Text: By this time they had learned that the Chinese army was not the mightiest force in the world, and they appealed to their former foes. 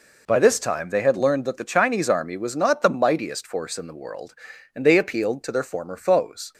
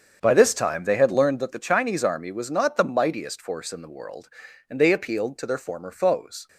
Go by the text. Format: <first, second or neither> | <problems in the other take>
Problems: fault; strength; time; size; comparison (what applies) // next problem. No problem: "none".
first | starts louder than the rest; strong; until 1.6 s; 7.5 dB